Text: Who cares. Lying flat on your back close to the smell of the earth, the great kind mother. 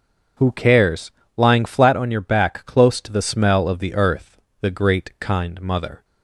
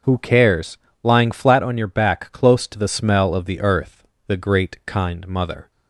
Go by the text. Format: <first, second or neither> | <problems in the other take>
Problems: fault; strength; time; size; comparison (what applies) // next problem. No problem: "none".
neither | starts louder than the rest; the same in both